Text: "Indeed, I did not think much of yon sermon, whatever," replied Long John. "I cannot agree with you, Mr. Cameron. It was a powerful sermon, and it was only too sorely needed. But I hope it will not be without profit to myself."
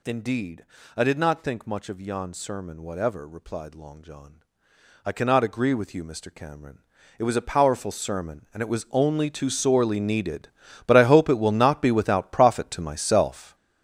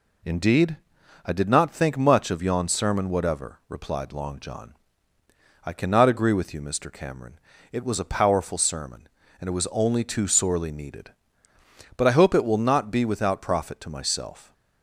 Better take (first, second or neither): second